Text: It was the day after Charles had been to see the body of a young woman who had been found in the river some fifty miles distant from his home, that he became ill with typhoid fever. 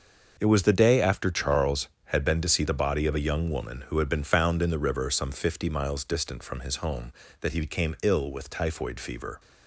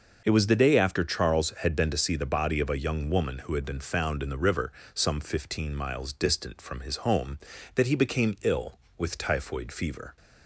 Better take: first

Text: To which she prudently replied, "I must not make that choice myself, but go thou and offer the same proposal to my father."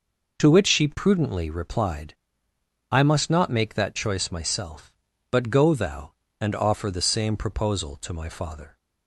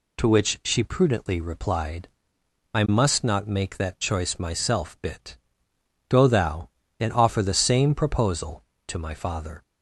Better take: first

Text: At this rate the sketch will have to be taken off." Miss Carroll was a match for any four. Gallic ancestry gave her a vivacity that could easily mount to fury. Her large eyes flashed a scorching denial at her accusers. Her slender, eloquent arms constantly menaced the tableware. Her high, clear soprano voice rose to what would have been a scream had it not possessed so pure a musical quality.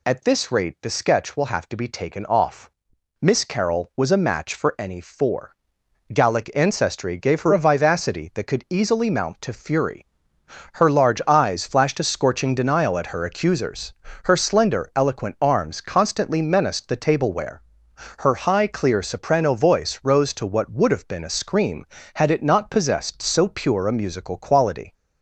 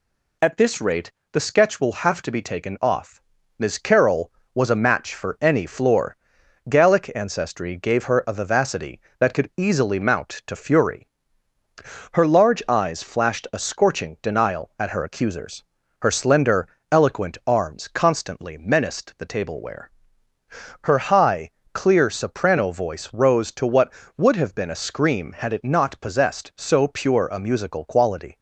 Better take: first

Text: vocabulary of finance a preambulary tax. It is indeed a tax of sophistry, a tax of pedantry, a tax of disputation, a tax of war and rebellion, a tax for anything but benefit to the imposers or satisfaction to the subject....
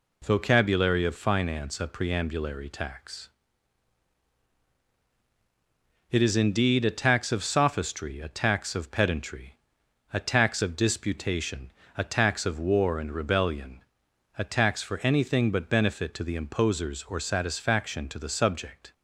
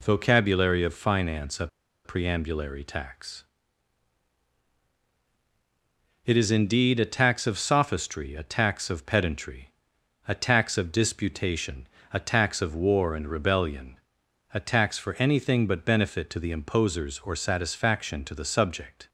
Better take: first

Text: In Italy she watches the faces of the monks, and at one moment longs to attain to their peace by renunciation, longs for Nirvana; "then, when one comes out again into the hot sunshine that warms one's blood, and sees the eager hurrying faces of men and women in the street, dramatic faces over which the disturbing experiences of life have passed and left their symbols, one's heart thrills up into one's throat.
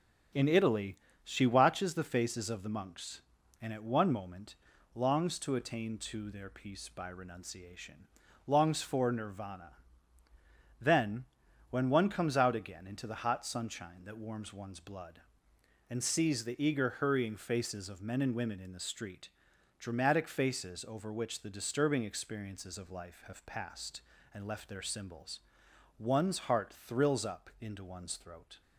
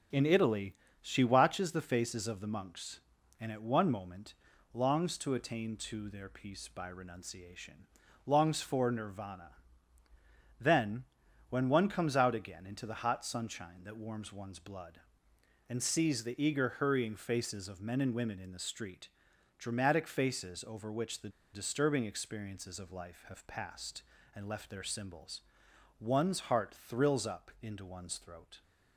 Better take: first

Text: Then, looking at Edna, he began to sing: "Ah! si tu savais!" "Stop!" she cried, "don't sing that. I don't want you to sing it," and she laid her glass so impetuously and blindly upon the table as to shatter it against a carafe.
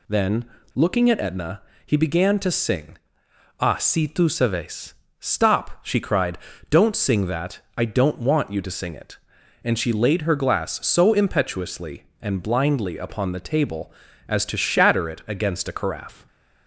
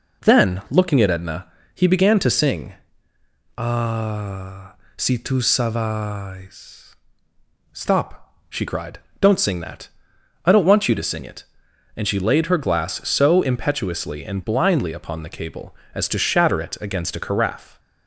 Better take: first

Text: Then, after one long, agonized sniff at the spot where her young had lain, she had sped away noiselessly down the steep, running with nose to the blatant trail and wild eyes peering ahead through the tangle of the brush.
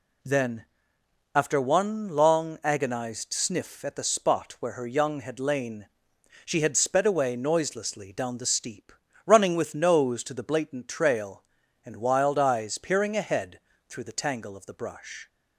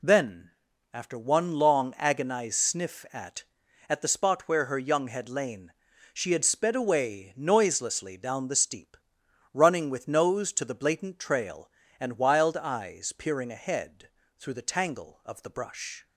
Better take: first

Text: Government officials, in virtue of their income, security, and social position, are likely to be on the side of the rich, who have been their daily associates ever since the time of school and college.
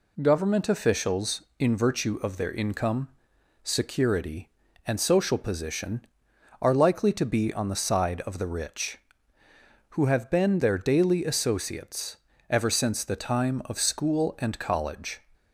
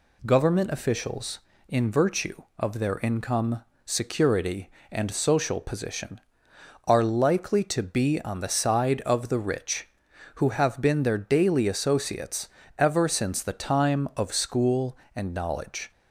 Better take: first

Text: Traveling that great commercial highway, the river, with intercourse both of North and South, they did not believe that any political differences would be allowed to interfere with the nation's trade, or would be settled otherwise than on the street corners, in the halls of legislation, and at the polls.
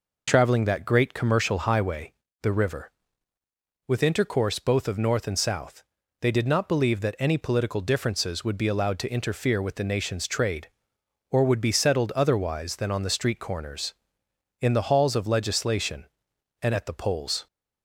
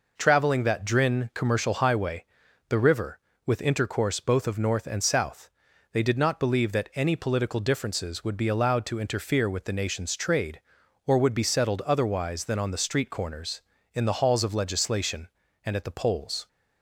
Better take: first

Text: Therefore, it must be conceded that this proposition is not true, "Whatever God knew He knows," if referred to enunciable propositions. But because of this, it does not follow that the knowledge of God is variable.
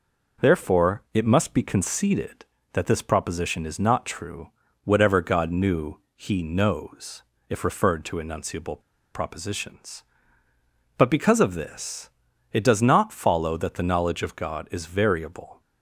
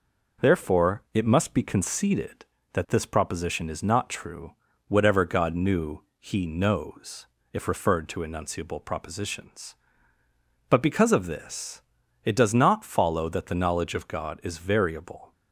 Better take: second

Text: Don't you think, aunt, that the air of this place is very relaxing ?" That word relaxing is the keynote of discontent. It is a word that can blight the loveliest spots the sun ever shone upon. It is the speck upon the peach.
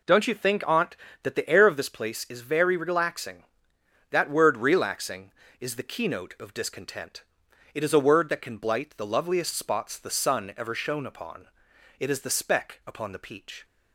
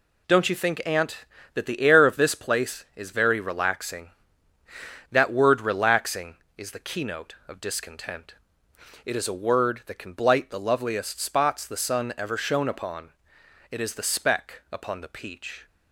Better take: neither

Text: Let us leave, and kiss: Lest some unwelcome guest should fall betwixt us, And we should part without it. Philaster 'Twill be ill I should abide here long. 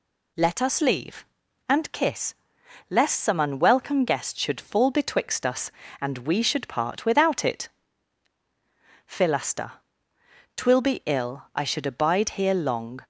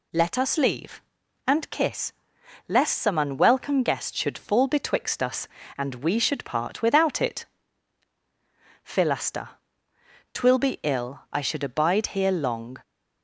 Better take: neither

